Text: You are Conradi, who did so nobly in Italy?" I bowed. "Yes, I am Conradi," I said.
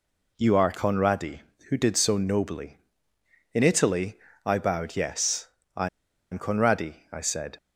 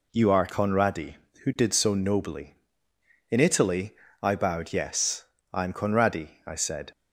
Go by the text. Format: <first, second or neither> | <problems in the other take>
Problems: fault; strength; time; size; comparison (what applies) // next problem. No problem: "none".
second | pauses between "I" and "am"; at 5.8 s; 0.45 s long